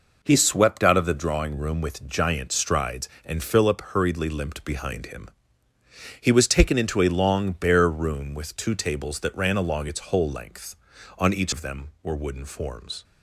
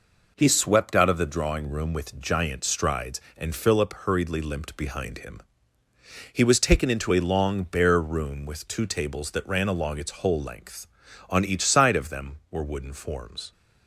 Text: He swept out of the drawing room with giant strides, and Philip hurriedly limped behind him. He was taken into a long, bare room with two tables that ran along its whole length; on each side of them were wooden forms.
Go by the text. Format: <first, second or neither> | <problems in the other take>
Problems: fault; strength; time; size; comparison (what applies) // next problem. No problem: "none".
second | skips "side"; at 11.5 s